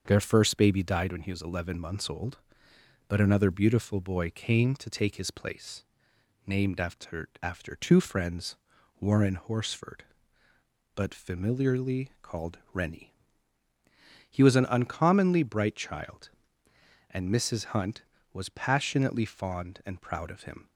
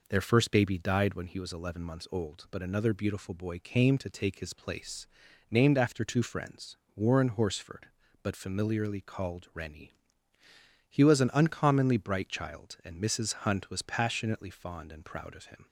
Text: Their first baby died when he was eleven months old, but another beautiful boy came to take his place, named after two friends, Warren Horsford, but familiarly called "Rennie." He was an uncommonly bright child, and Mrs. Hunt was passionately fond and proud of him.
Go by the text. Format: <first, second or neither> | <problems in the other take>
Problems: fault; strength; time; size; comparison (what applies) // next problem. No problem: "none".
second | starts louder than the rest; until 1.0 s; 6.5 dB // says "after" twice; at 7.4 s